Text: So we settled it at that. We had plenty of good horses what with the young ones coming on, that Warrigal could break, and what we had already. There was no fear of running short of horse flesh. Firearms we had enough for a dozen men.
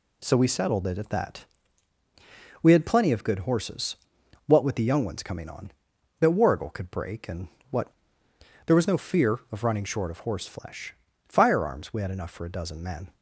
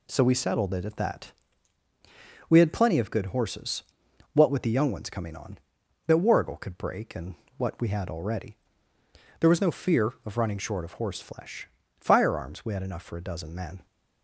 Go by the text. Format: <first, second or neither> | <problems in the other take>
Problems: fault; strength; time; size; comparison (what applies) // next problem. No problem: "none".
second | pauses between "horses" and "what"; noticeable; at 3.9 s; 0.50 s long; noticeable in the second // pauses between "and" and "what"; slight; at 7.4 s; 0.22 s long; slight in the second // skips "we had already"; at 8.2 s